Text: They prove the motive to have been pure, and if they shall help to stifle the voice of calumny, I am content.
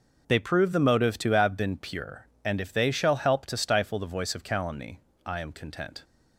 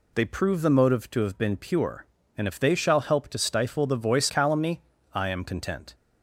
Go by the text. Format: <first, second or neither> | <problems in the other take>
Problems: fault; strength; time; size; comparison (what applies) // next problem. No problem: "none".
first | skips "of"; at 4.2 s